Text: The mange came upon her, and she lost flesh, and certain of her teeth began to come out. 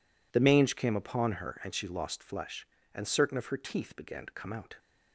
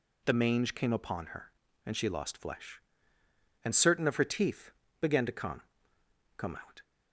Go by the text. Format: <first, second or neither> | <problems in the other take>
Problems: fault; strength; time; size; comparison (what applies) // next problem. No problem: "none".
first | pauses between "teeth" and "began"; slight; at 4.7 s; 0.30 s long // says "come" twice; at 6.3 s